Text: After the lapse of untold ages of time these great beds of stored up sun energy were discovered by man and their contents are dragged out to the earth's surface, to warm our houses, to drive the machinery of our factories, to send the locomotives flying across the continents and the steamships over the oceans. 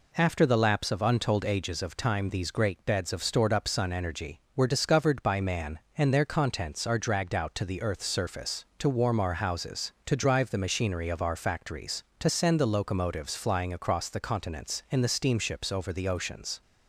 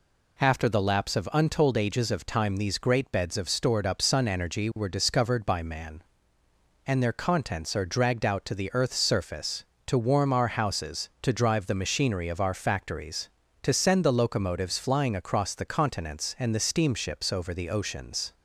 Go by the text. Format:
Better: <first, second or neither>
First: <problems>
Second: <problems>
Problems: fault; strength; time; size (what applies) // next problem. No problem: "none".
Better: neither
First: none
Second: none